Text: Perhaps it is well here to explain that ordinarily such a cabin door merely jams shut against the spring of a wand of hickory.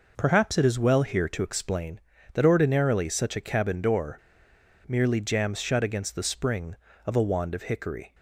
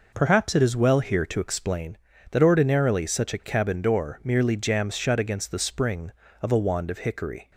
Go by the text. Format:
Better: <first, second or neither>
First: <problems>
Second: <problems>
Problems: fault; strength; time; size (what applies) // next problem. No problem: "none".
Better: second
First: pauses between "door" and "merely"; noticeable; at 4.1 s; 0.70 s long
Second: none